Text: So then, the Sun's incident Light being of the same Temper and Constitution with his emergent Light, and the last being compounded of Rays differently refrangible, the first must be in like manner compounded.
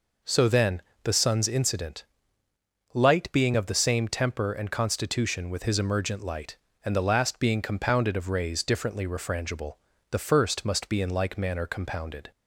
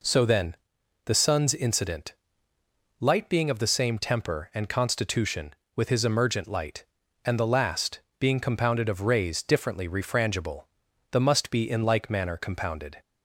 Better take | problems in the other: first | pauses between "incident" and "Light"; noticeable; at 2.1 s; 0.86 s long; noticeable in the first // pauses between "last" and "being"; slight; at 8.0 s; 0.18 s long // skips "first"; at 11.2 s

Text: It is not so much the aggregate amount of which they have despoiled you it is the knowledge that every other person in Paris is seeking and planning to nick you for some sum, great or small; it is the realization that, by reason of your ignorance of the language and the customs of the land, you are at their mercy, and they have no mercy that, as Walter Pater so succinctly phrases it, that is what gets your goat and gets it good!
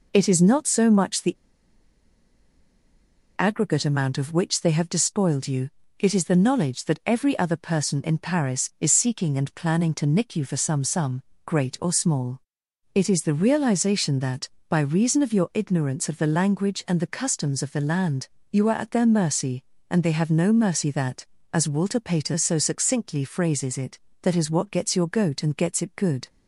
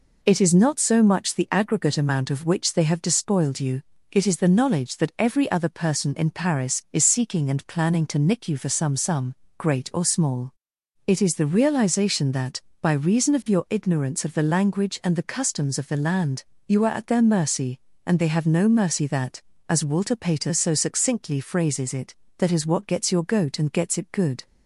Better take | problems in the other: second | pauses between "the" and "aggregate"; strong; at 1.3 s; 2.0 s long // pauses between "you" and "it"; slight; at 5.6 s; 0.30 s long; slight in the second

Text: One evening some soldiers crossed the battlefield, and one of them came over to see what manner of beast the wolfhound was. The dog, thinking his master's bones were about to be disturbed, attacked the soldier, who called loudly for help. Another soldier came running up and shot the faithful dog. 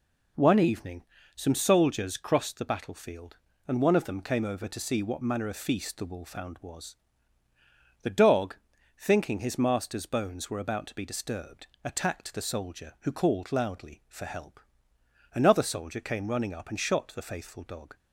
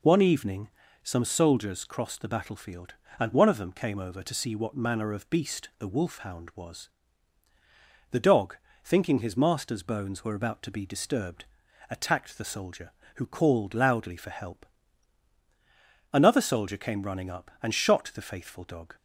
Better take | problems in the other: second | pauses between "evening" and "some"; slight; at 1.0 s; 0.30 s long; slight in the second // says "feast" for "beast"; at 5.5 s

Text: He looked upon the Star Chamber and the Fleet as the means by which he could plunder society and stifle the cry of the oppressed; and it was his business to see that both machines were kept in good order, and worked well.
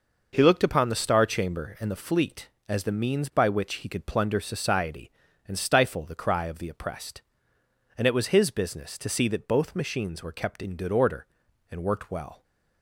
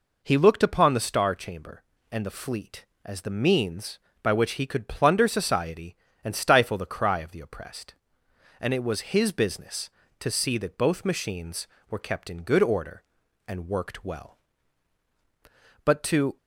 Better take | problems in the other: first | goes on to say "But to"; from 15.8 s on; 0.52 s long

